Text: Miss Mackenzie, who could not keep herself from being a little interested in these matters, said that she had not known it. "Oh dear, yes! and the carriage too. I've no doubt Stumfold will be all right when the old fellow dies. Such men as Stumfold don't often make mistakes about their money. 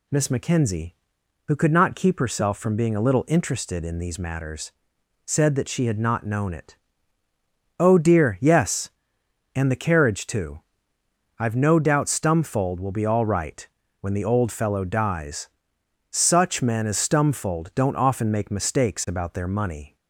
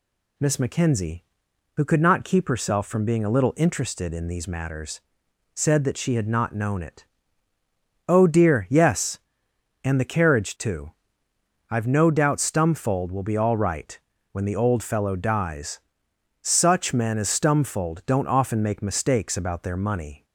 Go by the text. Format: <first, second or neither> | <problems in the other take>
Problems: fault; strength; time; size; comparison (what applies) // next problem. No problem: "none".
neither | pauses between "right" and "when"; slight; the same in both